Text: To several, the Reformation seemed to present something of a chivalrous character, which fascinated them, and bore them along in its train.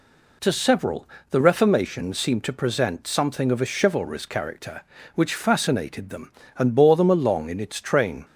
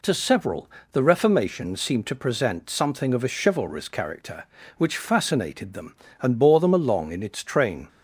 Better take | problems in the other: neither | none

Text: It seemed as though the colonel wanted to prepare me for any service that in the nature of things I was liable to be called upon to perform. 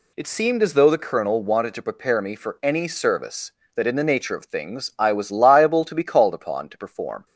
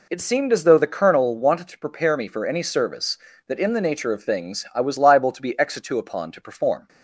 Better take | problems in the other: first | says "exitu" for "called"; at 5.5 s

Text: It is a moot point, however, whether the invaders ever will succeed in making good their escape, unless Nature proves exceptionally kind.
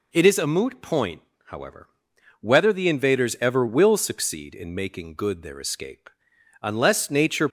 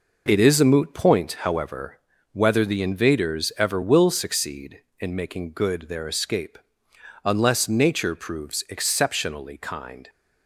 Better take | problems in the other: second | stops before "proves exceptionally kind"; at 7.4 s

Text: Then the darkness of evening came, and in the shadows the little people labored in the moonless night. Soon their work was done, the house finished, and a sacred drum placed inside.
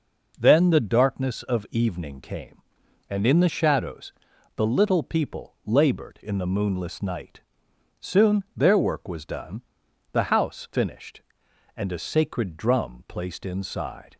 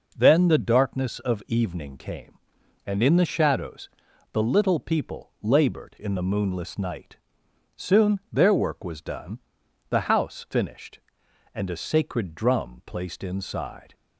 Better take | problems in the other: neither | pauses between "shadows" and "the"; the same in both

